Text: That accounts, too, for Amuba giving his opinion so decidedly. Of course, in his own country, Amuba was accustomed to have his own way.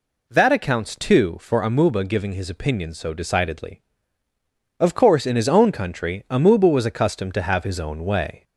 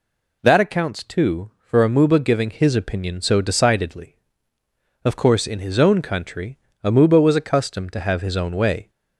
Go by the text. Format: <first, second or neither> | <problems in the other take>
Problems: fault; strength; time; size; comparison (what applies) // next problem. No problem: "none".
neither | none